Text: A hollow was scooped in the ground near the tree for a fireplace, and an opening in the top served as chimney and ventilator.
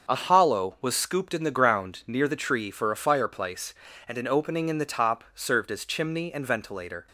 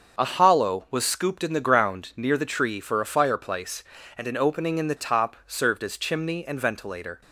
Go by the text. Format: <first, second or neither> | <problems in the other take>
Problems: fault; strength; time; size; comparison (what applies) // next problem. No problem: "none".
neither | starts louder than the rest; the same in both